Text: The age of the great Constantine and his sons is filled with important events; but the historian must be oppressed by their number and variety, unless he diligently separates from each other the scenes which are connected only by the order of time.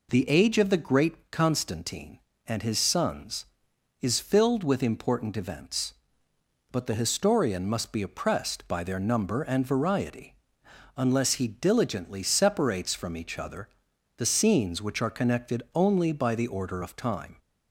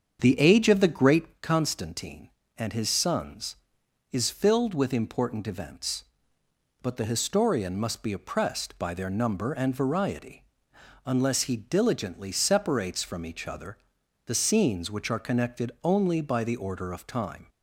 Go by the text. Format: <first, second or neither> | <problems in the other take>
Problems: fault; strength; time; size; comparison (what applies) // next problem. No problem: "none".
first | starts louder than the rest; strong; until 1.5 s; 7.5 dB // pauses between "other" and "the"; noticeable; at 13.7 s; 0.48 s long; noticeable in the first